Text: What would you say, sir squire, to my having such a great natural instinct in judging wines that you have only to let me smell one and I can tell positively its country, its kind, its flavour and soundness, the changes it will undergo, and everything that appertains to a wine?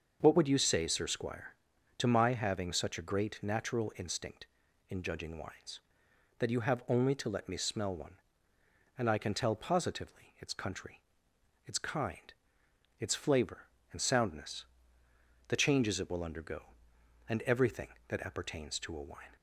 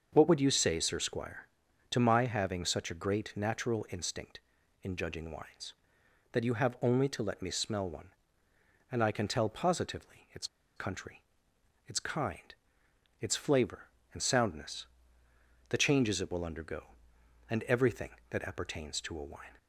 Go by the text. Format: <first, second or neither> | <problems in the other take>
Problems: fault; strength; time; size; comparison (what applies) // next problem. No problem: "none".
first | starts louder than the rest; until 1.1 s; 6.5 dB; also in the first // pauses between "its" and "country"; slight; at 10.4 s; 0.30 s long